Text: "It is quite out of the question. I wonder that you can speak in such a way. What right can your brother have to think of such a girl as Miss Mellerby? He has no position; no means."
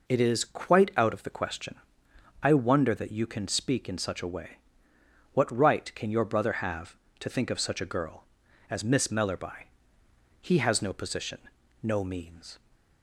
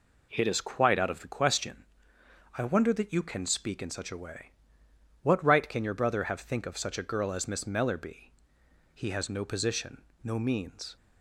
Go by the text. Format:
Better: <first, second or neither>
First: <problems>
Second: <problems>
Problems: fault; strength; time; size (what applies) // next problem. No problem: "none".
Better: first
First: none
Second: skips "to"; at 6.3 s